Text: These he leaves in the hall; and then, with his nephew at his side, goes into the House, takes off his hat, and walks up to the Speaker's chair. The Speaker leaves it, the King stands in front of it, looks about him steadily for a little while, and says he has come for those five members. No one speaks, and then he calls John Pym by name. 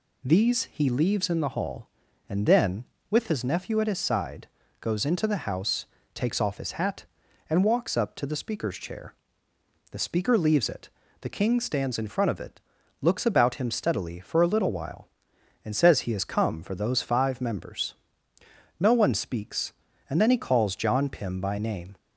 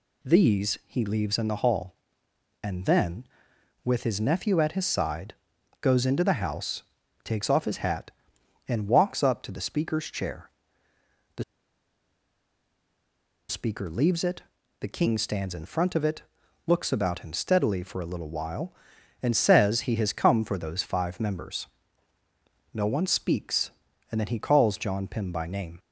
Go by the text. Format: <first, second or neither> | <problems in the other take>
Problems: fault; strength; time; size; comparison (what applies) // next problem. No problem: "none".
first | pauses between "The" and "Speaker"; strong; at 11.4 s; 2.0 s long